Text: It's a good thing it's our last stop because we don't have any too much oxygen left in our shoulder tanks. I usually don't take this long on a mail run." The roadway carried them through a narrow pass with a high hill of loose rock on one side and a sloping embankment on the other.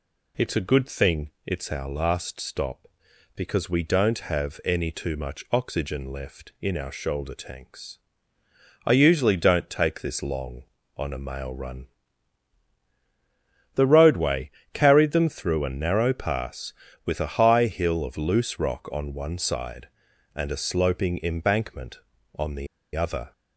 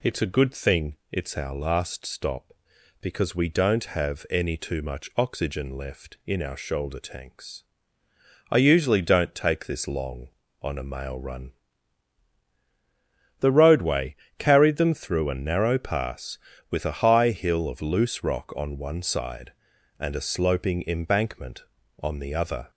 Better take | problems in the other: second | pauses between "thing" and "it's"; slight; at 1.2 s; 0.16 s long; slight in the second // pauses between "roadway" and "carried"; slight; at 14.4 s; 0.24 s long; slight in the second // pauses between "the" and "other"; slight; at 22.6 s; 0.29 s long

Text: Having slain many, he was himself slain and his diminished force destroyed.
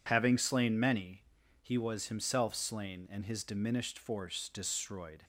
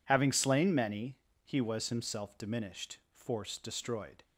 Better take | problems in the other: first | skips "slain and his"; at 2.3 s // pauses between "diminished" and "force"; slight; at 2.9 s; 0.16 s long

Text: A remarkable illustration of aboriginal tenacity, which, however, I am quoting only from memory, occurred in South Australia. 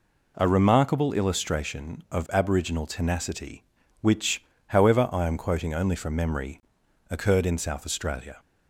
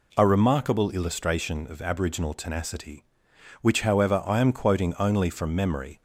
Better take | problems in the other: first | stops before "occurred in South Australia"; at 5.9 s

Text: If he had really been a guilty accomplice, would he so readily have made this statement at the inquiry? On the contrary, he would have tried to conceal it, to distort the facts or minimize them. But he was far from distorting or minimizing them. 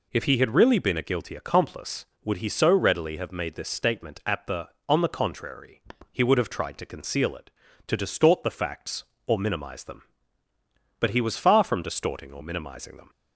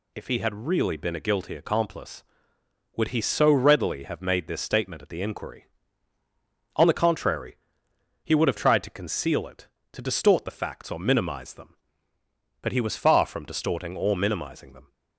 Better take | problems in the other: second | skips "inquiry"; at 4.7 s

